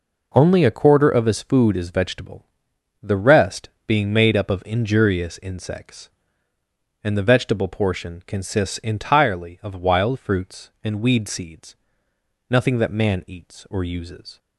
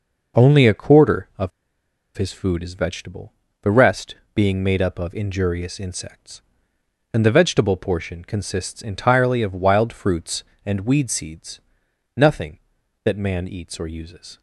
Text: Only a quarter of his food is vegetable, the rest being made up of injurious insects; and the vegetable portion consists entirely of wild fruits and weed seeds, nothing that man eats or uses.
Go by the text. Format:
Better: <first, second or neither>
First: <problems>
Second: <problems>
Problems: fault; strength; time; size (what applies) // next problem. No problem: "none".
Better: first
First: pauses between "rest" and "being"; slight; at 3.6 s; 0.16 s long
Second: pauses between "of" and "his"; noticeable; at 1.5 s; 0.67 s long // pauses between "rest" and "being"; slight; at 4.1 s; 0.18 s long